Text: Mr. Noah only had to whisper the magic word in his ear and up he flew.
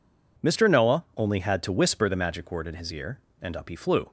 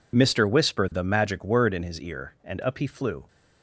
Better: first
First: none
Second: skips "Noah only had to"; at 0.4 s

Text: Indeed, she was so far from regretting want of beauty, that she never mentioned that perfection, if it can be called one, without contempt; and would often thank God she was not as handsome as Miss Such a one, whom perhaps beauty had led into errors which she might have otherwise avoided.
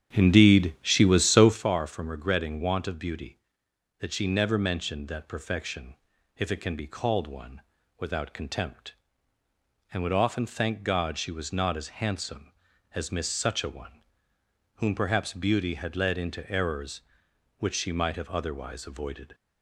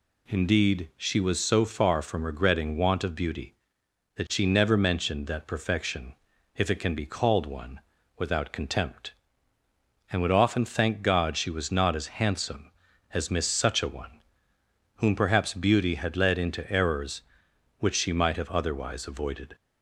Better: second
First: starts louder than the rest; strong; until 1.6 s; 9 dB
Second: none

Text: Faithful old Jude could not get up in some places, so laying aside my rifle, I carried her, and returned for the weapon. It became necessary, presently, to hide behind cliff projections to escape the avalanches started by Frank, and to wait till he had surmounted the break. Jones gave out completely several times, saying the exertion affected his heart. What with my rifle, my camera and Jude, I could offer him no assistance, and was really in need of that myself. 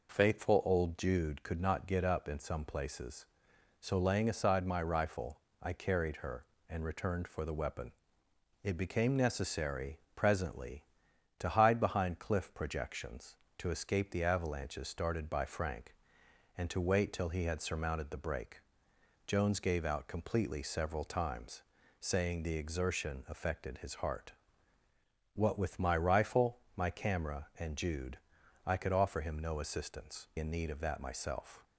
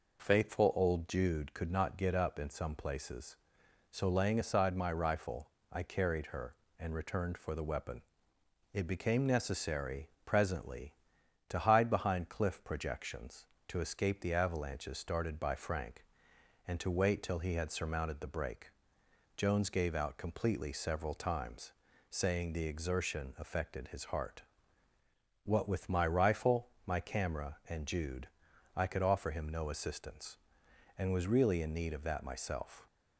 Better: second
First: skips "and was really"; at 30.3 s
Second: none

